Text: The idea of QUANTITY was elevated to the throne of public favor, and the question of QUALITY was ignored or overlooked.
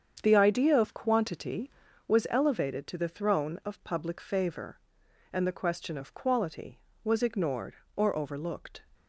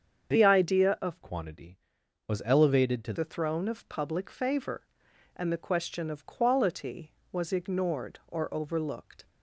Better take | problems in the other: first | starts louder than the rest; strong; until 1.3 s; 7 dB; strong in the first // changes voice from "QUANTITY" to "to"; from 1.2 to 3.1 s; 1.9 s long

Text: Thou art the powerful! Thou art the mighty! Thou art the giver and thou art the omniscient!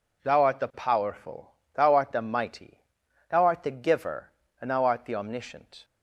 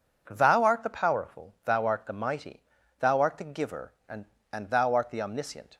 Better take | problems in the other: first | says "and" twice; at 4.5 s

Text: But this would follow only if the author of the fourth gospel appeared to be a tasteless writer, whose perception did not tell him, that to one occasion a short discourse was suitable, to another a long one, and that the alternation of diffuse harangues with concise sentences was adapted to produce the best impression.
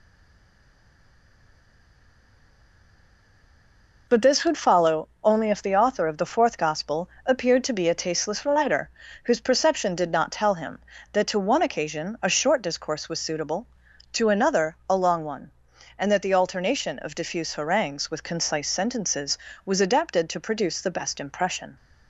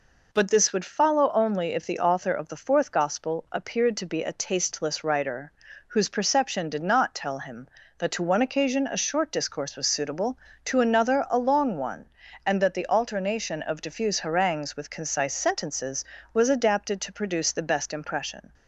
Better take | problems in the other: second | stays silent before the first word; strong; until 4.0 s; 4.0 s long // pauses between "gospel" and "appeared"; slight; at 7.0 s; 0.16 s long

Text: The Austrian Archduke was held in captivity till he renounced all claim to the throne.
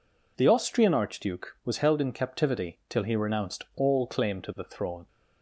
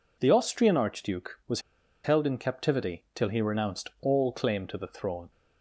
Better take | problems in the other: first | pauses between "was" and "held"; at 1.5 s; 0.44 s long

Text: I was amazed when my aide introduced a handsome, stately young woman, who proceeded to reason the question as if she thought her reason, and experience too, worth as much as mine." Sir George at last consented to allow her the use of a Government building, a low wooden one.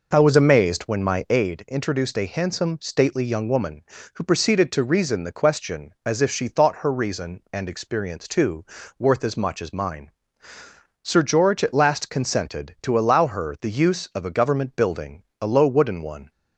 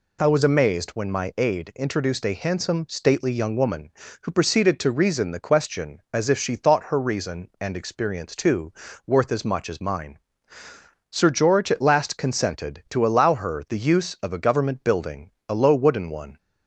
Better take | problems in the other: second | starts louder than the rest; noticeable; until 1.6 s; 5 dB

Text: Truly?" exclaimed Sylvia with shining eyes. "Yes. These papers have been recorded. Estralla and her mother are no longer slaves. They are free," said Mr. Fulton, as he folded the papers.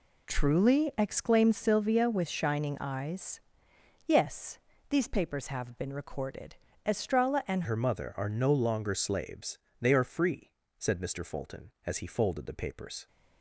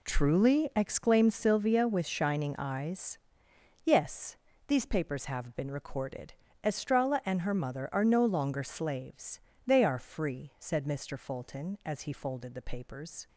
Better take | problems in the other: second | changes voice at "her"; from 7.6 s on; 5.4 s long

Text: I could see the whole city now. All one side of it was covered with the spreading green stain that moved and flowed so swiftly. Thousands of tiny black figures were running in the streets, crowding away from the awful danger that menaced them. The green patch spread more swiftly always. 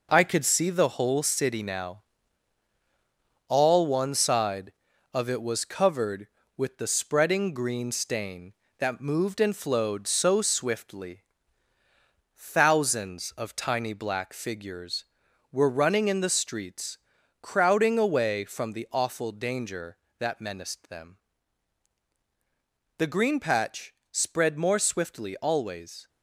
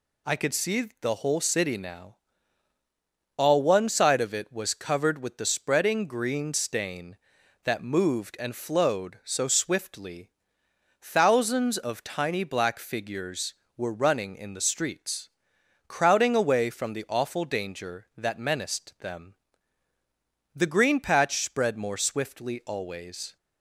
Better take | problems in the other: second | gets quieter; strong; throughout; 7.5 dB // pauses between "patch" and "spread"; slight; at 23.9 s; 0.16 s long

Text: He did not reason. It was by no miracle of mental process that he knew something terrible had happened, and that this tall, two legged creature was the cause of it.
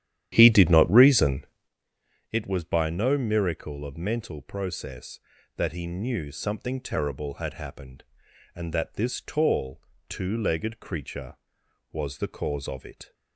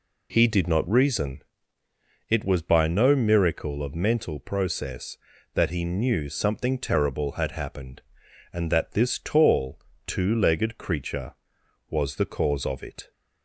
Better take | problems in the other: second | starts louder than the rest; strong; until 1.7 s; 11 dB

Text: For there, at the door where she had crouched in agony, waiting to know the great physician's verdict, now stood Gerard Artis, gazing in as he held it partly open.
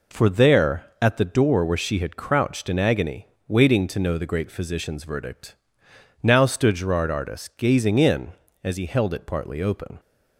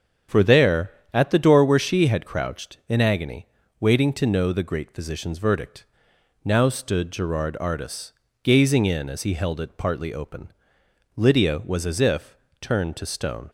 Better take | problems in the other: first | starts louder than the rest; strong; until 1.5 s; 7 dB // goes on to say "Lydia was as if turned to stone"; strong; from 11.1 s on; 2.3 s long

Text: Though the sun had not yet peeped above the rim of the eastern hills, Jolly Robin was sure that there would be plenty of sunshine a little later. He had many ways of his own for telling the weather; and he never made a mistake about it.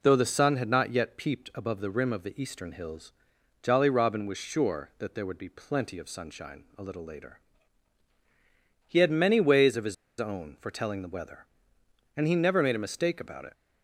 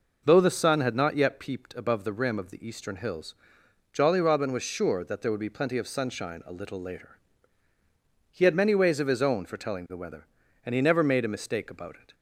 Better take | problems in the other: second | pauses between "his" and "own"; slight; at 9.9 s; 0.25 s long

